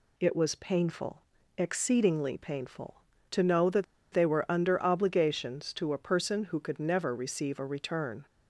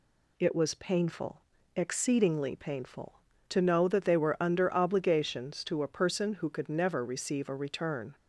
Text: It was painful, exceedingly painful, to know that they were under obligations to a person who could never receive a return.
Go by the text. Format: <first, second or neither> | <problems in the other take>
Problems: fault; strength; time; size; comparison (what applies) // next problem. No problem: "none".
second | pauses between "that" and "they"; slight; at 3.8 s; 0.27 s long